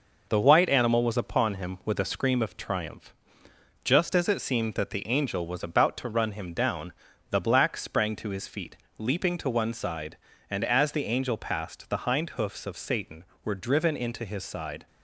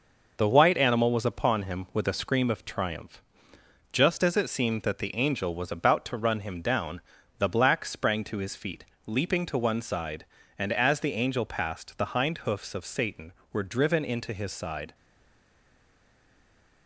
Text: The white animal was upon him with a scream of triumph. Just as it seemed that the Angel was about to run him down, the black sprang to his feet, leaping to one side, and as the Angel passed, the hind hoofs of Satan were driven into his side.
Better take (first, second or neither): first